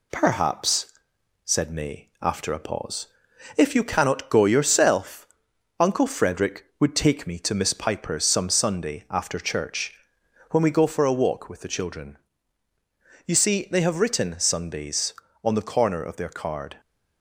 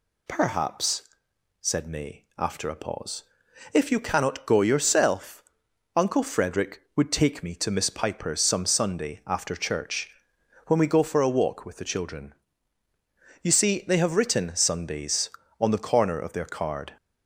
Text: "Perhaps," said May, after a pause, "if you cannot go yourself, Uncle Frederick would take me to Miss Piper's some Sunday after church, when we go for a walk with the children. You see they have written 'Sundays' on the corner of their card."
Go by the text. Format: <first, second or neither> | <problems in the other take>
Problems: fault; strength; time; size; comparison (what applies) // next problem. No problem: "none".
second | gets quieter; slight; throughout; 2.5 dB